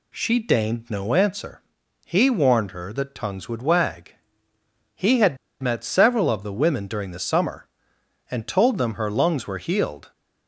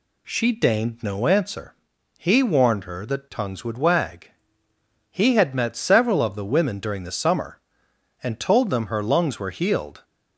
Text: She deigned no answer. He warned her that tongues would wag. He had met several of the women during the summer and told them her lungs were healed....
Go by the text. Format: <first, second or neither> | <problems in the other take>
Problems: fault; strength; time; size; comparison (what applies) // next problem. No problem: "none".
second | pauses between "had" and "met"; slight; at 5.3 s; 0.24 s long